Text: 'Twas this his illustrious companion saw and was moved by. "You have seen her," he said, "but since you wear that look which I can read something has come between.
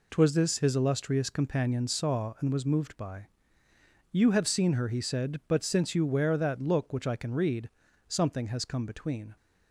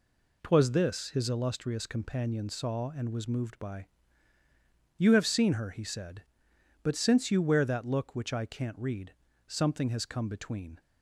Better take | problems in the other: first | says "can't" for "can"; at 8.4 s // pauses between "read" and "something"; slight; at 9.1 s; 0.32 s long; also in the first

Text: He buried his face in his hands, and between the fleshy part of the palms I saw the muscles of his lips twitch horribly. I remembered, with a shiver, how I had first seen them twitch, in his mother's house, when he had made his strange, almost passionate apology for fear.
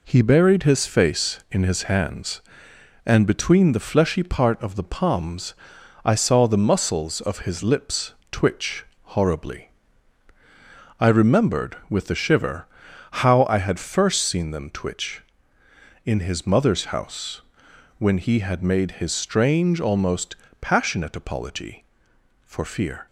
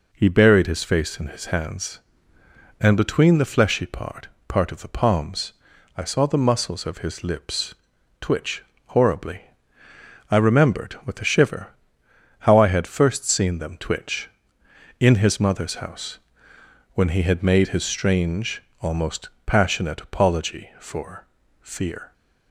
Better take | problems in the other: first | says "part" twice; at 4.4 s // pauses between "palms" and "I"; at 5.5 s; 0.44 s long; noticeable in the first // pauses between "lips" and "twitch"; noticeable; at 7.7 s; 0.46 s long; slight in the first // pauses between "twitch" and "horribly"; slight; at 8.6 s; 0.24 s long; slight in the first // pauses between "almost" and "passionate"; slight; at 19.2 s; 0.16 s long; slight in the first // pauses between "for" and "fear"; slight; at 21.2 s; 0.34 s long

